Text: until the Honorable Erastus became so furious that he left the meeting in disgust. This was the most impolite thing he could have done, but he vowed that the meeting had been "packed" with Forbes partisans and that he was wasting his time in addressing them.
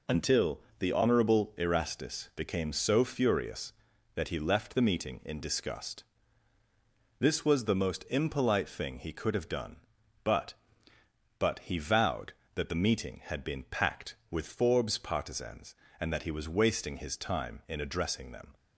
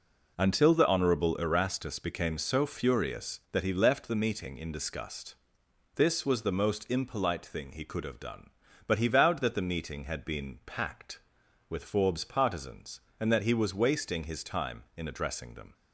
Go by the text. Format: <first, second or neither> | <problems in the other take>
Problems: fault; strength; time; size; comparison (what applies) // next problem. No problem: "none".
second | pauses between "until" and "the"; slight; at 0.5 s; 0.18 s long // says "but" twice; at 11.3 s